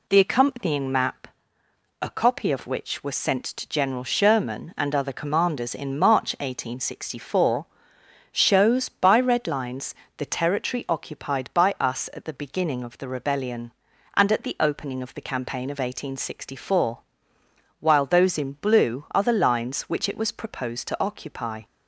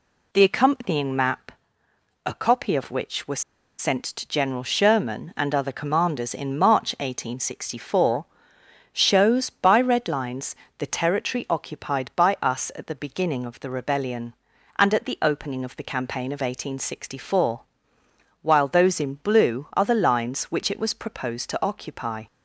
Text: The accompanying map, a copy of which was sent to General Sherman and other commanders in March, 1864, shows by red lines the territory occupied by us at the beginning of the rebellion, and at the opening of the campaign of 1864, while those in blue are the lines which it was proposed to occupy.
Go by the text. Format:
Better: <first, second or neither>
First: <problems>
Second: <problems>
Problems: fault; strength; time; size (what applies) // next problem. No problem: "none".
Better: first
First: pauses between "lines" and "the"; slight; at 9.9 s; 0.22 s long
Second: pauses between "was" and "sent"; at 3.4 s; 0.37 s long // pauses between "lines" and "the"; slight; at 10.5 s; 0.22 s long